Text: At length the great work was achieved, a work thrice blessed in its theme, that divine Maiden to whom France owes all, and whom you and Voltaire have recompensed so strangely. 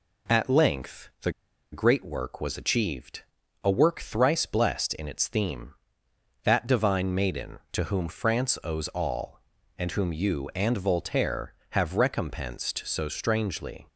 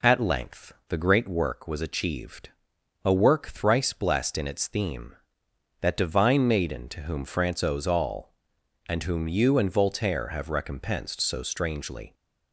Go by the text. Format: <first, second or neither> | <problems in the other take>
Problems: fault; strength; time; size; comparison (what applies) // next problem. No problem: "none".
second | pauses between "the" and "great"; at 1.3 s; 0.41 s long